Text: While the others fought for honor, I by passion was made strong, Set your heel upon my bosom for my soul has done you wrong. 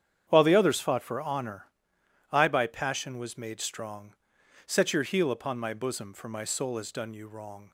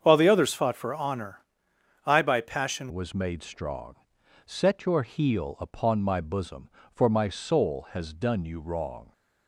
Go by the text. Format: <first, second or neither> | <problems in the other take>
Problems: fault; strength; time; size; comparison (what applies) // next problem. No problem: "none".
first | starts louder than the rest; strong; until 1.0 s; 7.5 dB; strong in the first // changes voice at "was"; from 2.9 s on; 6.2 s long